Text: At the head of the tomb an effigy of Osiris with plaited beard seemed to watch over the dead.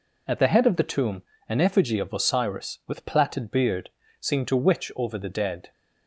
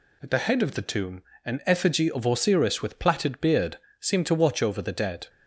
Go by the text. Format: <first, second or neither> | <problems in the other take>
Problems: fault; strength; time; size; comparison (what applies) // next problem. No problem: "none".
second | pauses between "tomb" and "an"; slight; at 1.2 s; 0.26 s long; slight in the second // pauses between "beard" and "seemed"; slight; at 3.8 s; 0.30 s long; slight in the second // says "witch" for "watch"; at 4.5 s